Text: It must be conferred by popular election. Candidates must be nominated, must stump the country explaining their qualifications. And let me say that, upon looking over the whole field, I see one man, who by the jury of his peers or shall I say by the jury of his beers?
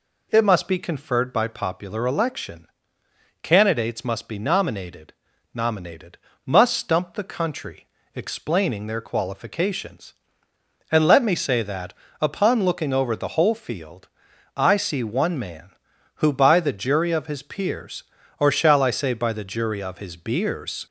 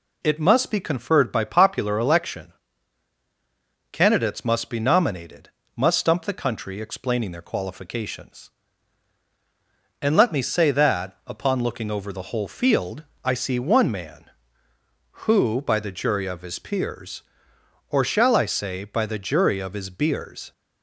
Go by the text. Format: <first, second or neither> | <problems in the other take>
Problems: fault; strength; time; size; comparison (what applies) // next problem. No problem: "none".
second | says "nominated" twice; at 5.5 s // pauses between "country" and "explaining"; slight; at 7.8 s; 0.26 s long